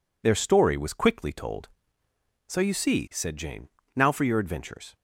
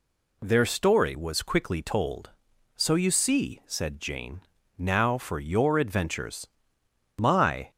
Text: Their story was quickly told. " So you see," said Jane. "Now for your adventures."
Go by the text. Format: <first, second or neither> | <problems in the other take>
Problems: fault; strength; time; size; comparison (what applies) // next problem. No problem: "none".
first | goes on to say "My"; from 7.1 s on; 0.52 s long